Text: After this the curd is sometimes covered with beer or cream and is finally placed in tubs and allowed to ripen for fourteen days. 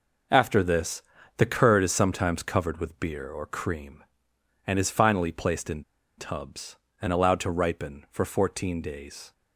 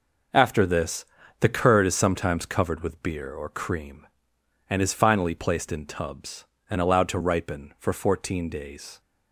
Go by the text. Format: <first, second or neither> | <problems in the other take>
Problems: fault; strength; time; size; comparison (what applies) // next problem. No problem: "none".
second | pauses between "this" and "the"; slight; at 1.0 s; 0.34 s long; slight in the second // pauses between "in" and "tubs"; slight; at 5.8 s; 0.35 s long